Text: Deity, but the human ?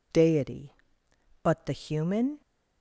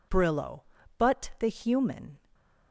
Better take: first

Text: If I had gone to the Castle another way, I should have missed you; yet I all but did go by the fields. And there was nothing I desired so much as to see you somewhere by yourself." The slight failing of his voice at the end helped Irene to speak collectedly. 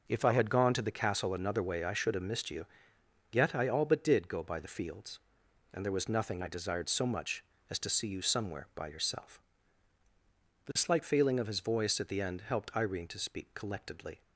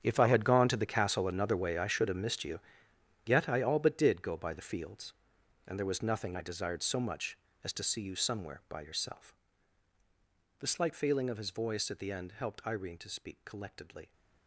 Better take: first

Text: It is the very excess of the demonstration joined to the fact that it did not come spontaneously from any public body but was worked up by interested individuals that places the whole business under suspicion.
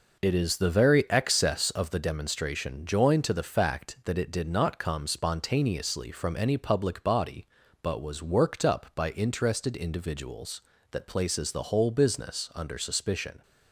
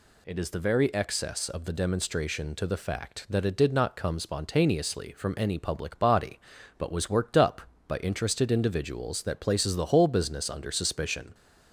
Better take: first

